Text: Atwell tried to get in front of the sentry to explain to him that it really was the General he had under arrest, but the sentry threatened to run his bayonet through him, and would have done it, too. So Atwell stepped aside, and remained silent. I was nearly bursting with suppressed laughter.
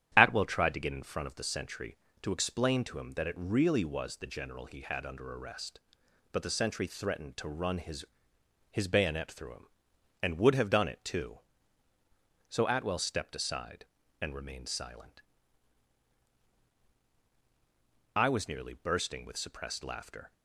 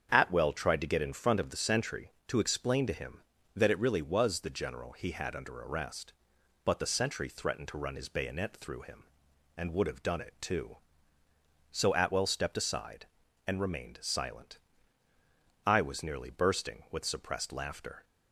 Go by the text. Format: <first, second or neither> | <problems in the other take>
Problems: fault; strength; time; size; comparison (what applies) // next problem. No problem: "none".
second | starts louder than the rest; strong; until 1.1 s; 10.5 dB; strong in the second // says "his" twice; at 8.7 s